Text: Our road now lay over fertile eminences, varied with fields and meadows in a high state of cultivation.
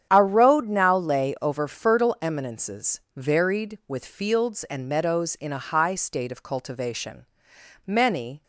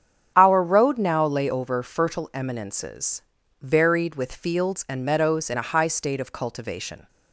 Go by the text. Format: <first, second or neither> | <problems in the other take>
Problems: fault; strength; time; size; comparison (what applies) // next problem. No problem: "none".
second | starts louder than the rest; strong; until 1.1 s; 9 dB; strong in the second // goes on to say "Many"; from 7.8 s on; 0.58 s long